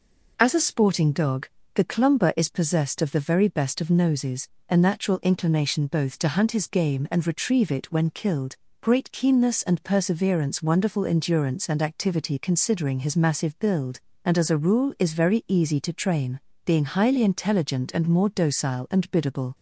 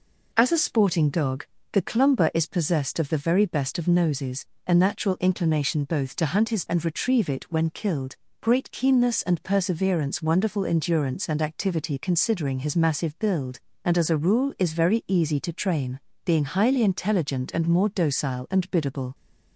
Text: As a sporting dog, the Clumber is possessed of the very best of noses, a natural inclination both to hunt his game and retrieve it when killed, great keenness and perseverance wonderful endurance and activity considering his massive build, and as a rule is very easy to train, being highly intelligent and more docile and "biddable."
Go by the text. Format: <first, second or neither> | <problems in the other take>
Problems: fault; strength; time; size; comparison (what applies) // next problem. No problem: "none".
first | skips "game"; at 6.6 s